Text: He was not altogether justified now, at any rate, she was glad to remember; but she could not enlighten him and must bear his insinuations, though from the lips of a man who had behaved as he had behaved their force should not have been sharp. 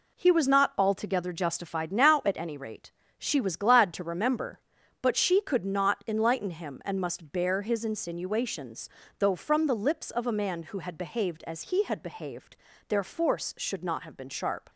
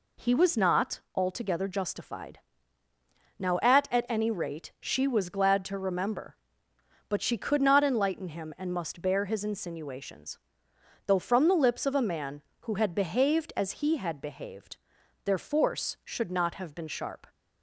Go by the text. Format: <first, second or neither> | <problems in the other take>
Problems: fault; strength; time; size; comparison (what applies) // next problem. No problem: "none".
first | pauses between "not" and "altogether"; slight; at 0.9 s; 0.16 s long // pauses between "justified" and "now"; at 2.3 s; 1.0 s long // says "at" twice; at 3.8 s // pauses between "behaved" and "their"; noticeable; at 14.7 s; 0.48 s long; slight in the first